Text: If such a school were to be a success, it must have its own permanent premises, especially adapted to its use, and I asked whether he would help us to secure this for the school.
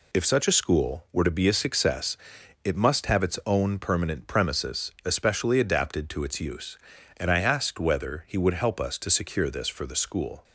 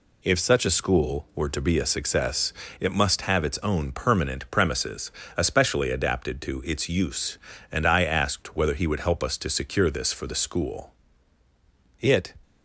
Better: first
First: none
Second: goes on to say "It"; slight; from 11.9 s on; 0.34 s long

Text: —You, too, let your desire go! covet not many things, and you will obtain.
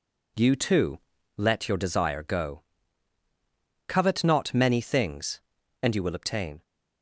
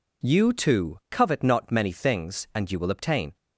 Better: first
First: none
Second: skips "let your desire go"; at 1.0 s

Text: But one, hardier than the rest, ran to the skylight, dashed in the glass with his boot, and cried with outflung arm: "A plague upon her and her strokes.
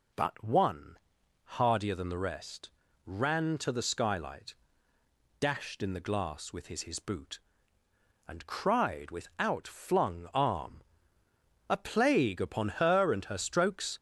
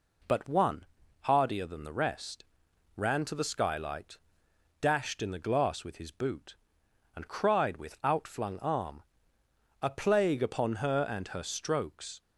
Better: second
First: says "his" twice; at 6.8 s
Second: none

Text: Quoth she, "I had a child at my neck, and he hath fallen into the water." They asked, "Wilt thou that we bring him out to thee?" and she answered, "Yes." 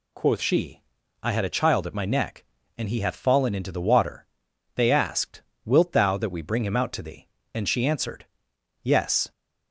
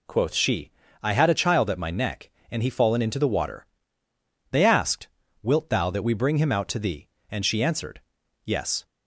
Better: first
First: none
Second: skips "hath"; at 2.6 s

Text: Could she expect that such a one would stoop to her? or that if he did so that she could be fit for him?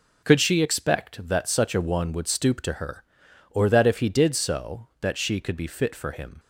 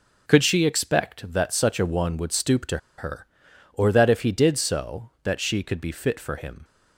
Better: first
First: none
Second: pauses between "to" and "her"; slight; at 2.7 s; 0.19 s long

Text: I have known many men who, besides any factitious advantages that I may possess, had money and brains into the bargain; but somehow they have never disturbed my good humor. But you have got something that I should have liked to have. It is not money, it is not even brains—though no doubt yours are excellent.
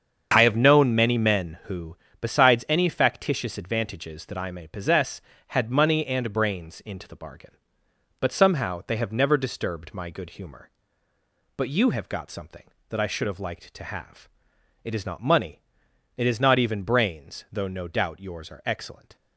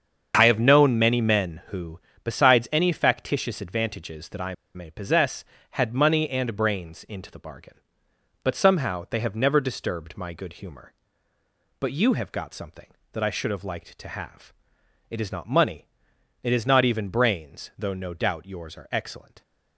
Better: first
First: starts louder than the rest; strong; until 1.3 s; 7 dB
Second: starts louder than the rest; strong; until 1.3 s; 7 dB // pauses between "I" and "may"; slight; at 4.5 s; 0.21 s long

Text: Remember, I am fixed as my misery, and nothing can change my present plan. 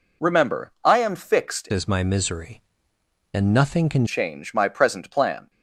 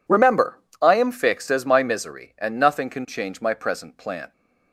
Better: second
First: changes voice from "as" to "can"; from 1.7 to 4.0 s; 2.3 s long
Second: none

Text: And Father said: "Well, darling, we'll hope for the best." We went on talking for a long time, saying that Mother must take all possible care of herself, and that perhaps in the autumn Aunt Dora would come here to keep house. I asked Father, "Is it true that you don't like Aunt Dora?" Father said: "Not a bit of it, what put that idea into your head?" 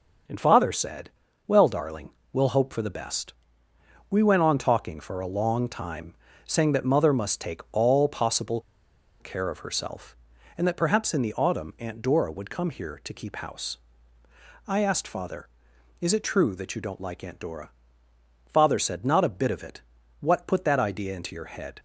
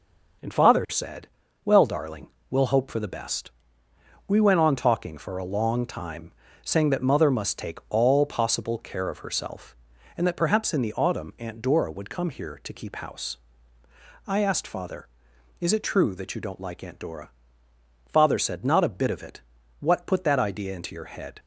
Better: second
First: starts louder than the rest; noticeable; until 1.6 s; 6 dB // pauses between "possible" and "care"; noticeable; at 8.5 s; 0.60 s long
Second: starts louder than the rest; noticeable; until 1.8 s; 6 dB

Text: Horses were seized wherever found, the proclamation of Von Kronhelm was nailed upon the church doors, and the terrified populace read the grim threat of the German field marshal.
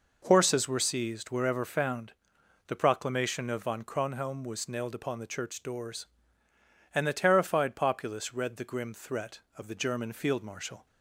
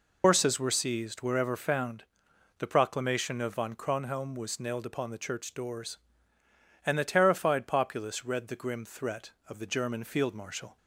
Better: first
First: none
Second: loses the start of "Horses"; at 0.2 s; 110 ms

